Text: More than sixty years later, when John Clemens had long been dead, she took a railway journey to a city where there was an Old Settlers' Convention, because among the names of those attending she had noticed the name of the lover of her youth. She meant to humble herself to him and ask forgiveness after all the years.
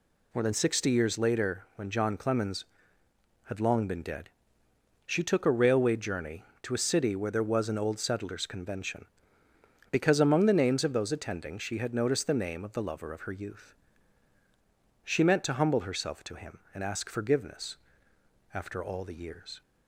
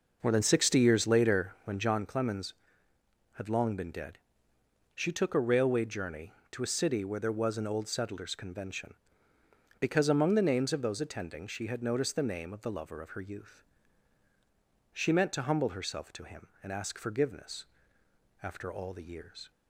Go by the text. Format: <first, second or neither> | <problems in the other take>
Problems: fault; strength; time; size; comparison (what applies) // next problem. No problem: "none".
first | starts louder than the rest; noticeable; until 2.0 s; 5.5 dB // pauses between "forgiveness" and "after"; noticeable; at 17.6 s; 0.78 s long; noticeable in the first